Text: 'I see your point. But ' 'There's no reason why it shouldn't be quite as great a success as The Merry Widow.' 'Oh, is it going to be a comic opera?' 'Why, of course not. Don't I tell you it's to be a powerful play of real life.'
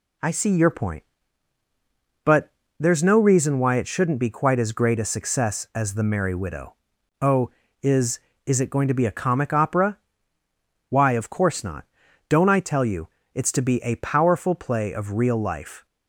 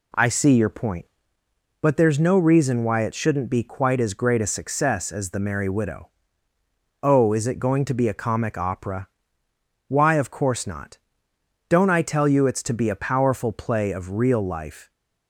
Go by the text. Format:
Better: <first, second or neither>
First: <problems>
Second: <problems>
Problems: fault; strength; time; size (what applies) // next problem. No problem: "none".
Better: second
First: says "is" twice; at 8.4 s // pauses between "you" and "it's"; slight; at 13.0 s; 0.26 s long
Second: none